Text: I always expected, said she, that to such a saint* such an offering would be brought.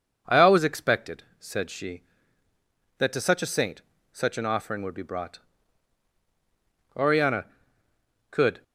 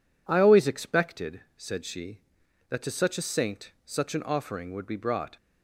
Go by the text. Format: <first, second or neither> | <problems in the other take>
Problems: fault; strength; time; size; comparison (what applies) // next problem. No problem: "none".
second | pauses between "saint" and "such"; slight; at 3.8 s; 0.32 s long // goes on to say "Oriana could"; strong; from 6.9 s on; 1.6 s long